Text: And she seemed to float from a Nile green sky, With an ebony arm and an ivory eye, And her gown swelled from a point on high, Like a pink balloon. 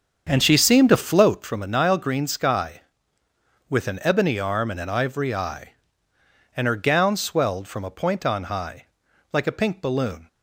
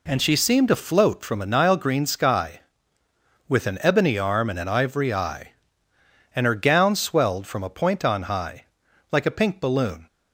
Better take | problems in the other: second | starts louder than the rest; strong; until 1.5 s; 7 dB

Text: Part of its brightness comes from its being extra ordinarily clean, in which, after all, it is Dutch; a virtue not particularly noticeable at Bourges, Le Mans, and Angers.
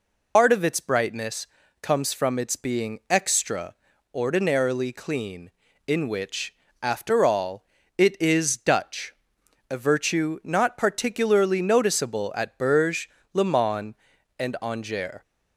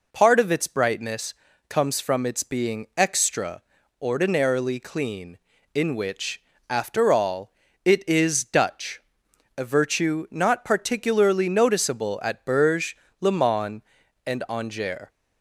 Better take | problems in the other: second | loses the start of "Part"; at 0.3 s; 100 ms // pauses between "brightness" and "comes"; slight; at 1.4 s; 0.34 s long; slight in the second // pauses between "extra" and "ordinarily"; at 3.7 s; 0.38 s long; also in the second

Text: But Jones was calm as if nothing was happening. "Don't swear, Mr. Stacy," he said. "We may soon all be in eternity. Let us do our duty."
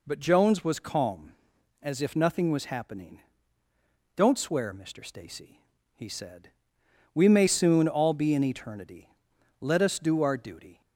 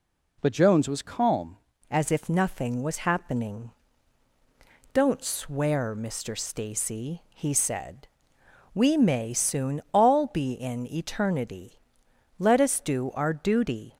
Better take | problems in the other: first | changes voice at "as"; from 1.8 s on; 12.1 s long

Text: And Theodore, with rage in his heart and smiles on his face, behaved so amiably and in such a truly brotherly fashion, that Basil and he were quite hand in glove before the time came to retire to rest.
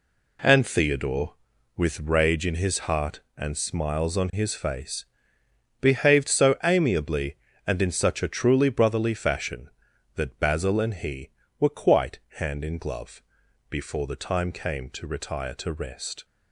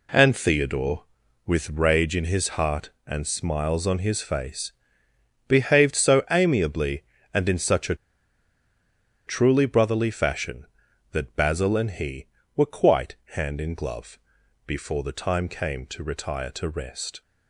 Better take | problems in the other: first | pauses between "a" and "truly"; strong; at 7.9 s; 1.3 s long // pauses between "quite" and "hand"; slight; at 13.1 s; 0.18 s long; slight in the first // pauses between "glove" and "before"; noticeable; at 14.1 s; 0.46 s long; noticeable in the first

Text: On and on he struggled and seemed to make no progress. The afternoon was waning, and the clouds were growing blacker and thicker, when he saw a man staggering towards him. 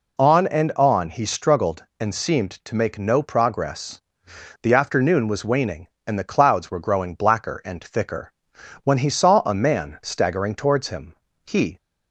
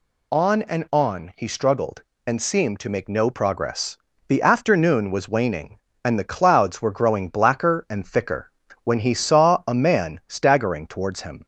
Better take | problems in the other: second | goes on to say "He"; slight; from 11.4 s on; 0.32 s long

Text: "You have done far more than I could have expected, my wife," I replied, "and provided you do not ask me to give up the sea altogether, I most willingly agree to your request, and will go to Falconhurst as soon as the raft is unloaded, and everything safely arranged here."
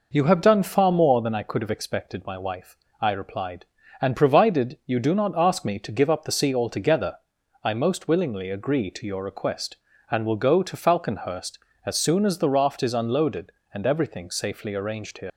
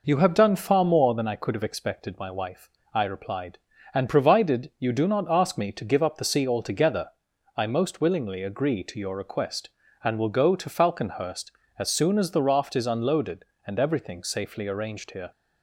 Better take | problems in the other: second | leaves "here" unfinished; at 15.3 s; 80 ms

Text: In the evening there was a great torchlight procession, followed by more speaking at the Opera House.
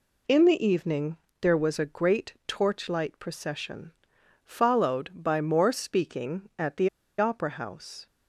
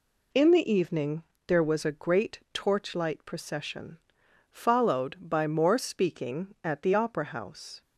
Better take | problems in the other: second | pauses between "evening" and "there"; slight; at 1.1 s; 0.24 s long; slight in the second // pauses between "the" and "Opera"; slight; at 6.8 s; 0.29 s long

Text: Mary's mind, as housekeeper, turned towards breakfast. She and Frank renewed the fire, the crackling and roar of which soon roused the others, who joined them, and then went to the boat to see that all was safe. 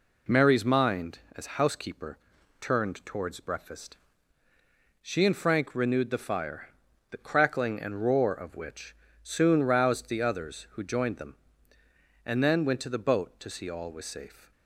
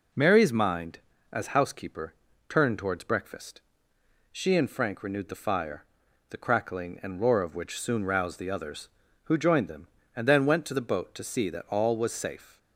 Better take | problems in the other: second | pauses between "which" and "soon"; slight; at 8.9 s; 0.30 s long // skips "that"; at 13.6 s

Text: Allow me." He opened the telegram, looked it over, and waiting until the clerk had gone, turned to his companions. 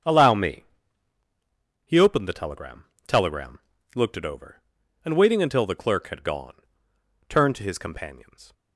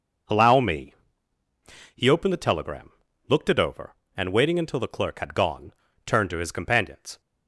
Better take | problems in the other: second | starts louder than the rest; strong; until 2.2 s; 7.5 dB // says "telegram" twice; at 3.0 s

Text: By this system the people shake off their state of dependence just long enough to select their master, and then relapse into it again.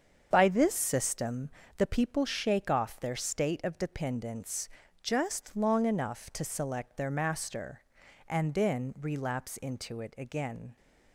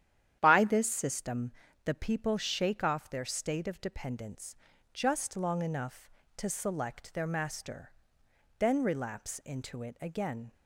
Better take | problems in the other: first | starts louder than the rest; strong; until 1.4 s; 10.5 dB; strong in the first // pauses between "system" and "the"; slight; at 1.5 s; 0.34 s long; slight in the first // pauses between "dependence" and "just"; at 4.5 s; 0.38 s long; slight in the first // skips "and"; at 8.2 s

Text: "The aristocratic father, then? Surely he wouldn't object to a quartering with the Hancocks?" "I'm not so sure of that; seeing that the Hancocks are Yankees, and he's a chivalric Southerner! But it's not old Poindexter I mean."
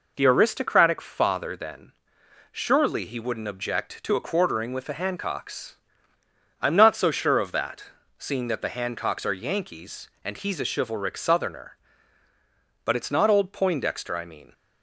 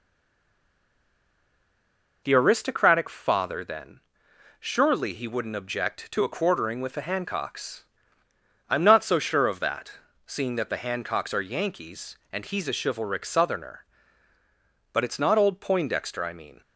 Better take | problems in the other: first | stays silent before the first word; until 2.2 s; 2.2 s long

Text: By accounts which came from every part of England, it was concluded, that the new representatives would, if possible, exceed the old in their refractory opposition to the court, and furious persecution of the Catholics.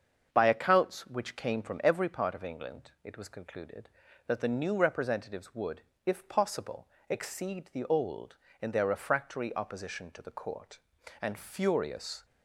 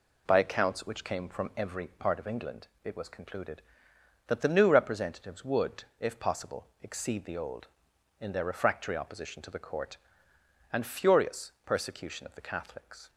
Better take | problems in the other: second | starts louder than the rest; until 1.3 s; 7 dB // stops before "persecution of the Catholics"; at 12.2 s

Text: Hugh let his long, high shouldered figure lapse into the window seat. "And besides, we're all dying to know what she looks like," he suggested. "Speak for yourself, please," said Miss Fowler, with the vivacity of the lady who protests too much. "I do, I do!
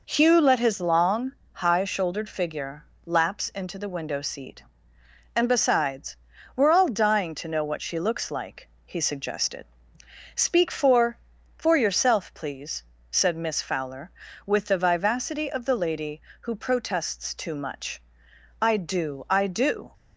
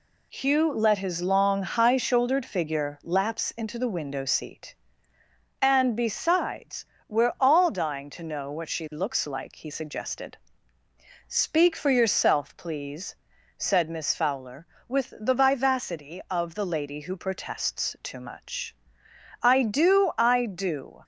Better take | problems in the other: second | pauses between "figure" and "lapse"; slight; at 2.8 s; 0.22 s long // says "for" twice; at 11.5 s

